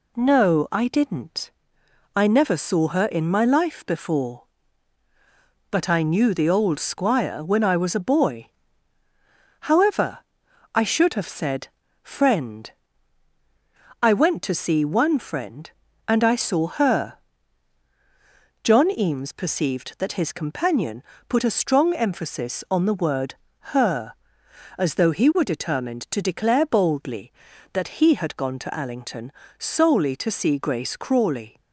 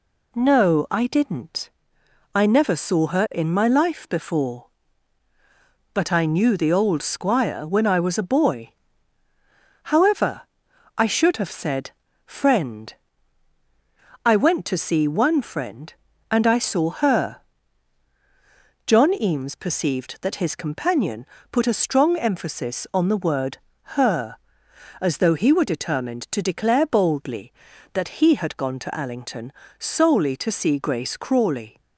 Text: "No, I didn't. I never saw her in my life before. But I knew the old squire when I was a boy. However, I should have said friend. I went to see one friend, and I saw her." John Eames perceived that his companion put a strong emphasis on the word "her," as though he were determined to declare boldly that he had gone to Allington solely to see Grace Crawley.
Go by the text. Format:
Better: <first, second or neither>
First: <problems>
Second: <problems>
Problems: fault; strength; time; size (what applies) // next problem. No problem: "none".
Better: neither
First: pauses between "said" and "friend"; slight; at 11.6 s; 0.36 s long // pauses between "companion" and "put"; slight; at 21.0 s; 0.26 s long // pauses between "word" and "her"; slight; at 23.3 s; 0.36 s long // pauses between "Allington" and "solely"; slight; at 29.3 s; 0.26 s long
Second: pauses between "said" and "friend"; slight; at 11.9 s; 0.36 s long // pauses between "companion" and "put"; slight; at 21.2 s; 0.26 s long // pauses between "word" and "her"; slight; at 23.5 s; 0.36 s long // pauses between "Allington" and "solely"; slight; at 29.5 s; 0.26 s long